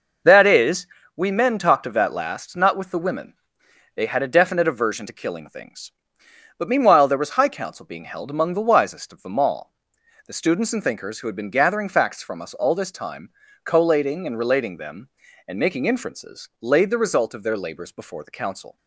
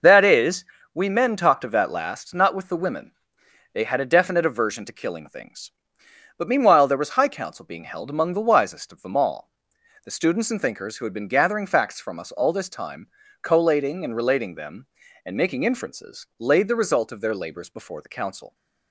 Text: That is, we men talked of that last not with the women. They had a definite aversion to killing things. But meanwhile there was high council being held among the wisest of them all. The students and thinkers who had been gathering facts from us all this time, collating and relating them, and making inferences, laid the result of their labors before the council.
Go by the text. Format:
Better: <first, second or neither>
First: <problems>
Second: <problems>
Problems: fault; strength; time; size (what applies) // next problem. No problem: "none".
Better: neither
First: none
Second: none